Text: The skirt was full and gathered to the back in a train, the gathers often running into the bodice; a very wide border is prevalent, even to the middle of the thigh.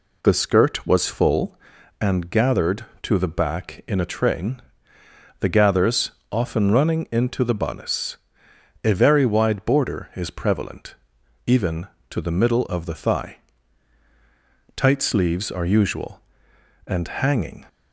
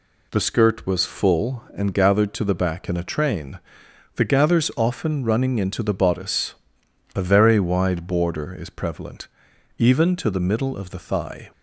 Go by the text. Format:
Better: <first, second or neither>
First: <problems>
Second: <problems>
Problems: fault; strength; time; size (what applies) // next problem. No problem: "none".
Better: second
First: pauses between "gathers" and "often"; slight; at 6.1 s; 0.20 s long // goes on to say "Tight sleeves are usual and hanging"; strong; from 14.7 s on; 2.9 s long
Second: none